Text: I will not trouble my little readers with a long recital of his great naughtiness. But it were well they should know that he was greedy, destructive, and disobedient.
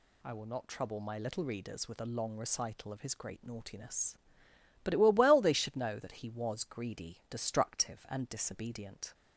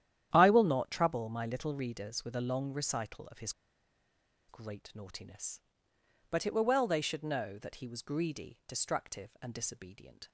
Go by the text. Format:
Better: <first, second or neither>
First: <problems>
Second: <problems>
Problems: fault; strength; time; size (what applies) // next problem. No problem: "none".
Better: first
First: none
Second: starts louder than the rest; strong; until 1.3 s; 11 dB // pauses between "his" and "great"; noticeable; at 3.5 s; 0.97 s long